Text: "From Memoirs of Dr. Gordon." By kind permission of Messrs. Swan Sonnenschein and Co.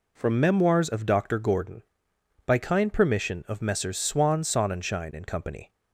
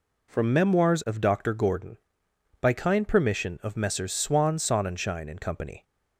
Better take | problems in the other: neither | none

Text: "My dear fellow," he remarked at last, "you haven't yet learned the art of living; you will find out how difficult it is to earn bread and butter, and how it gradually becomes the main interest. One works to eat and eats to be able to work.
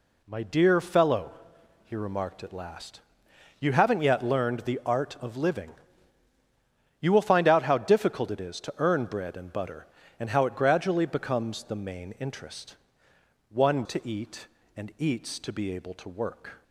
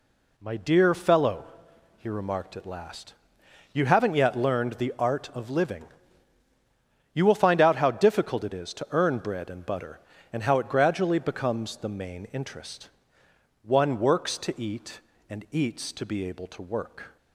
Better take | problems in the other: second | skips "works"; at 13.8 s

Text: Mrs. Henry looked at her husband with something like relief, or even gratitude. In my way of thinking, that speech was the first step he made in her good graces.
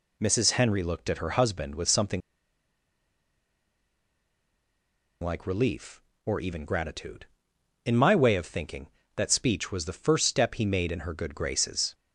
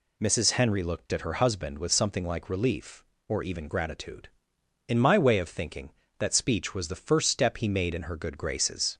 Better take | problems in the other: second | pauses between "something" and "like"; strong; at 2.2 s; 3.0 s long

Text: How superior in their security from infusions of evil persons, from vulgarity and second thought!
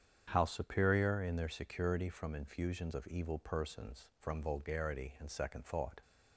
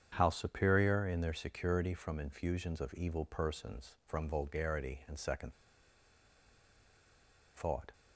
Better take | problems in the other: first | starts louder than the rest; strong; until 1.1 s; 8 dB; strong in the first // pauses between "second" and "thought"; strong; at 5.5 s; 2.0 s long

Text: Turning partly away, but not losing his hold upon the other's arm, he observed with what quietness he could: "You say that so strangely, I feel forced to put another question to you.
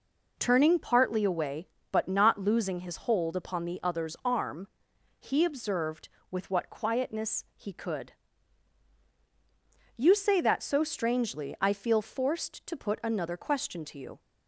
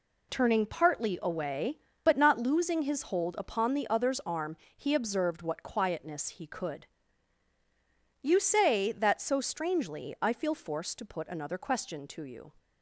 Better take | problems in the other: first | skips "with"; at 5.4 s

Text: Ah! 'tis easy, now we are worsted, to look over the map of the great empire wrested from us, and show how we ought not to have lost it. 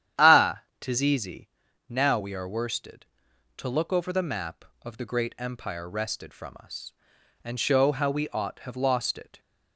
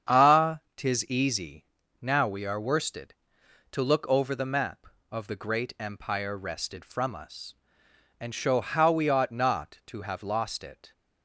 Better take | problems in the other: second | starts louder than the rest; strong; until 1.3 s; 10 dB; strong in the second // skips "not to"; at 8.5 s

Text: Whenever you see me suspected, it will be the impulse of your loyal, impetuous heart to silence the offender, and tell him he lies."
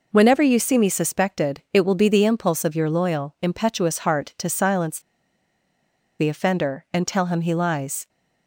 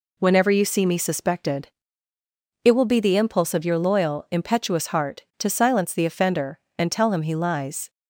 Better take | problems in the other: second | pauses between "silence" and "the"; at 4.9 s; 1.1 s long

